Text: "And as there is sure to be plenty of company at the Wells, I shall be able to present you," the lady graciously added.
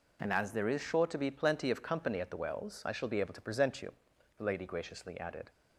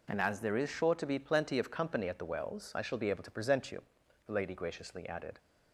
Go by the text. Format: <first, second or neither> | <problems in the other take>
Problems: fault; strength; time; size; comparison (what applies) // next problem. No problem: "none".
neither | none